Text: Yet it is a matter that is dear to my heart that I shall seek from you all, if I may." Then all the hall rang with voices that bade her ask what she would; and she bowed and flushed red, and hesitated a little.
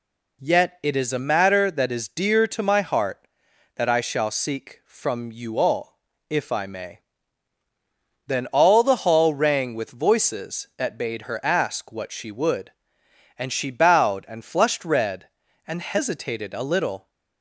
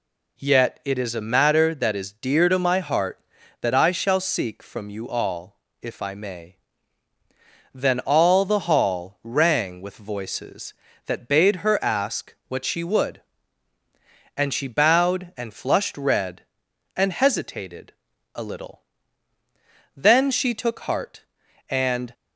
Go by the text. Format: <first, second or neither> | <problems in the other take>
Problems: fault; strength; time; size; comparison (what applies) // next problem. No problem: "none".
first | pauses between "hesitated" and "a"; at 17.9 s; 0.42 s long // goes on to say "Then she took heart and"; strong; from 19.9 s on; 2.1 s long